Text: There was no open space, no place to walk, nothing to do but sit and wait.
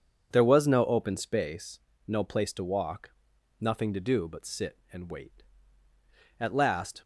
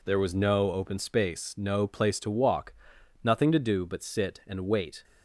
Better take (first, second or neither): second